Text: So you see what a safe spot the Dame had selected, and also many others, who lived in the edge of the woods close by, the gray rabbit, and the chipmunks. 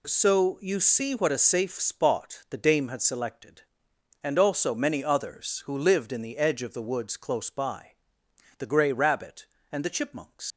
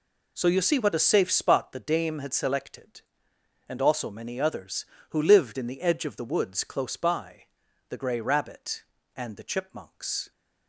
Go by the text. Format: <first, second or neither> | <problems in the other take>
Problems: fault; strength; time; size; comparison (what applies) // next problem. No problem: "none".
second | leaves "chipmunks" unfinished; at 10.5 s; 110 ms